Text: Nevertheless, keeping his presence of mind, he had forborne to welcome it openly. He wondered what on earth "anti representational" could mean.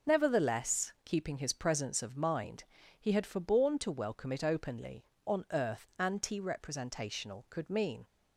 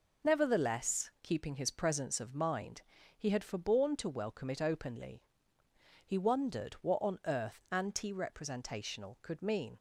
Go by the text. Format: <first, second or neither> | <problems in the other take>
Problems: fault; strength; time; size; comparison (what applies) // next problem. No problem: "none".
second | skips "He wondered what"; at 5.1 s